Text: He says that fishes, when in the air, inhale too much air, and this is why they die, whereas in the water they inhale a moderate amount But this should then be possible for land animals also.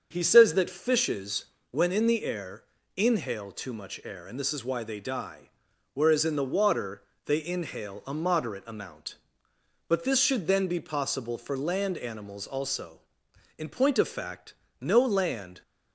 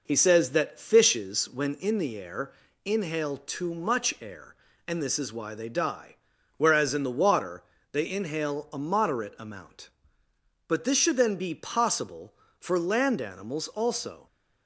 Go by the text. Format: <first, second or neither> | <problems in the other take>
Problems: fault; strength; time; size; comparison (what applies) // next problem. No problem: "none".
second | starts louder than the rest; until 1.1 s; 6.5 dB // pauses between "water" and "they"; slight; at 7.0 s; 0.22 s long; slight in the second // goes on to say "In point of fact no land"; strong; from 13.5 s on; 2.0 s long